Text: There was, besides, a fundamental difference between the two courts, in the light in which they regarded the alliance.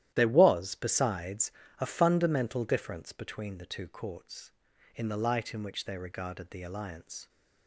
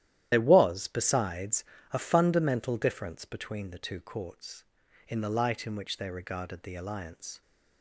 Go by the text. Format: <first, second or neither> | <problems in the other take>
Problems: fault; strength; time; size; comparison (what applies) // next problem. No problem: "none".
first | loses the start of "There"; at 0.3 s; 55 ms // starts louder than the rest; strong; until 1.3 s; 12 dB; strong in the first